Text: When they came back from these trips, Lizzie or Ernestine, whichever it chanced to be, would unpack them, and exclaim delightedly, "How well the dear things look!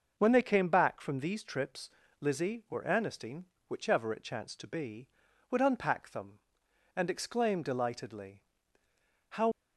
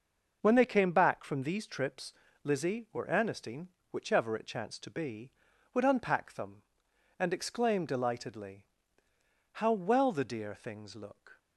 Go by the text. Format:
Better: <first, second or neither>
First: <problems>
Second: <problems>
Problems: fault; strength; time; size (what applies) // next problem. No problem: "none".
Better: second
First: stops before "well the dear things look"; at 9.5 s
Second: none